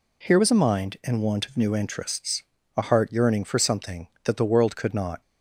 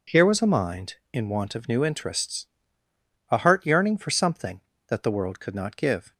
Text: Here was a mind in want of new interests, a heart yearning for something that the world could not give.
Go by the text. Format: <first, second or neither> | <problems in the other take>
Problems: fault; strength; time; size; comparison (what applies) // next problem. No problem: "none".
second | stops before "give"; at 5.2 s